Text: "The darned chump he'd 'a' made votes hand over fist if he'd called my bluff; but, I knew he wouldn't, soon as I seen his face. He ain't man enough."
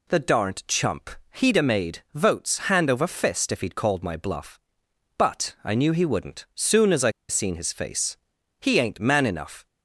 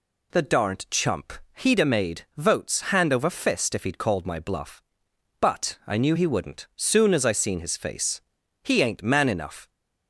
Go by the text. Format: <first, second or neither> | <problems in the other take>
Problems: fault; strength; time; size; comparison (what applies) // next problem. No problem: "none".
second | pauses between "chump" and "he'd"; slight; at 1.0 s; 0.24 s long; slight in the second // pauses between "I" and "seen"; slight; at 7.1 s; 0.17 s long